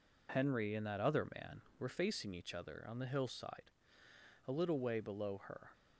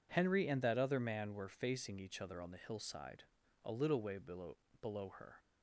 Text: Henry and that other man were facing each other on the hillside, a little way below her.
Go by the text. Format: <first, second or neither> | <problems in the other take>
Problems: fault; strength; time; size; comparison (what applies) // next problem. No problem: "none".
first | says "below" twice; at 4.8 s